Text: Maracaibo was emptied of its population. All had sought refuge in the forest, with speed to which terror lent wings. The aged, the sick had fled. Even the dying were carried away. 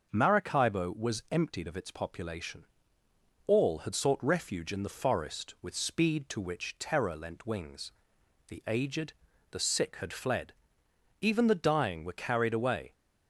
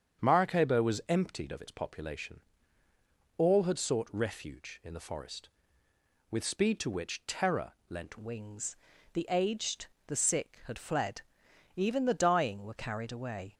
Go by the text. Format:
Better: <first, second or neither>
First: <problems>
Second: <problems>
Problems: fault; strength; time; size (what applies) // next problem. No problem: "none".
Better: first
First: starts louder than the rest; until 1.1 s; 6 dB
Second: starts louder than the rest; strong; until 1.2 s; 7.5 dB // pauses between "terror" and "lent"; slight; at 7.7 s; 0.16 s long // changes voice at "wings"; from 8.1 s on; 5.4 s long